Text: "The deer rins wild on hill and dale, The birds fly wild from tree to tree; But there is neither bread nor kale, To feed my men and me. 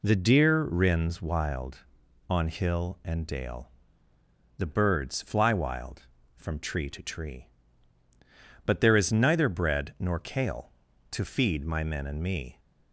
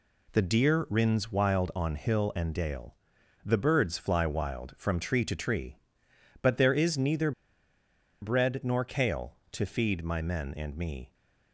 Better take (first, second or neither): first